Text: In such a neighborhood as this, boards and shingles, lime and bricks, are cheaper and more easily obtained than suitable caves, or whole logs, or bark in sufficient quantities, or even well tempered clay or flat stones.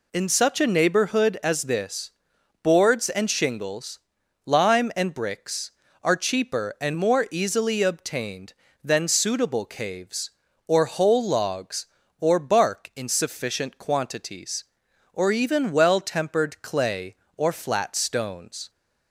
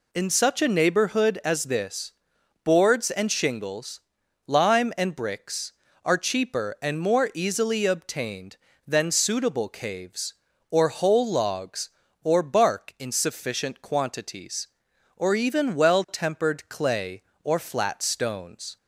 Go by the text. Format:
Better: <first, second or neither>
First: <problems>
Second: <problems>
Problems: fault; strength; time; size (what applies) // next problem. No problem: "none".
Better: neither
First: none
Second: none